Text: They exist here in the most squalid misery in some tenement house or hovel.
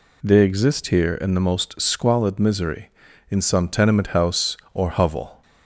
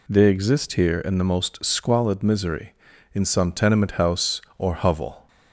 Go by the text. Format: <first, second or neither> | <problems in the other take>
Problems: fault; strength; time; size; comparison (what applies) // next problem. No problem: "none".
neither | none